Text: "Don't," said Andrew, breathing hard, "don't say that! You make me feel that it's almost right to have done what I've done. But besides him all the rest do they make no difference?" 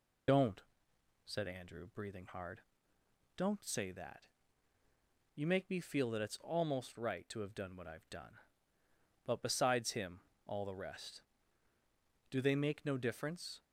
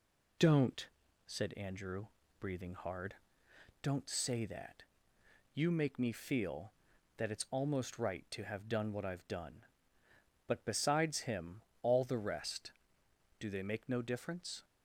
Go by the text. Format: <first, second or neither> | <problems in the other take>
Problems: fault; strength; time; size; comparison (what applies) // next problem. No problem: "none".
second | loses the start of "Don't"; at 0.2 s; 50 ms // pauses between "him" and "all"; slight; at 10.2 s; 0.24 s long; slight in the second